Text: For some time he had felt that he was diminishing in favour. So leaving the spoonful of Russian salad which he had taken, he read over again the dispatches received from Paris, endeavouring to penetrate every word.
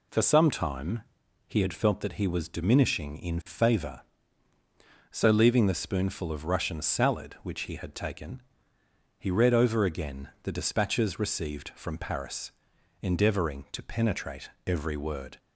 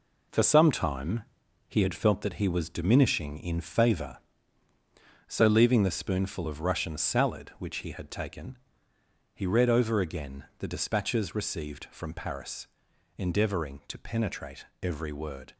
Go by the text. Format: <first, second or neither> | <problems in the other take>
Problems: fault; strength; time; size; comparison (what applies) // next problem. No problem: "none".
first | gets quieter; throughout; 6.5 dB // pauses between "time" and "he"; at 1.2 s; 0.44 s long; also in the first // pauses between "penetrate" and "every"; slight; at 14.6 s; 0.16 s long; slight in the first